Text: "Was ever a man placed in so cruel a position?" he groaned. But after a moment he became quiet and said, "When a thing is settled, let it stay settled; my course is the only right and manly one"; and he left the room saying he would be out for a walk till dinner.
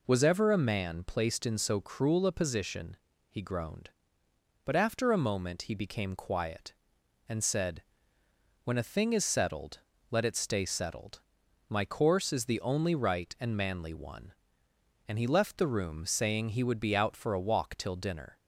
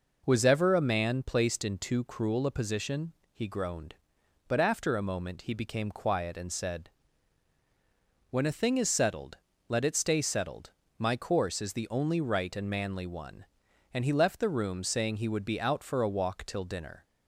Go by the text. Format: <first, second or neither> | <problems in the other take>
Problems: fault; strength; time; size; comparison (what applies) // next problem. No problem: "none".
first | says "too" for "so"; at 1.7 s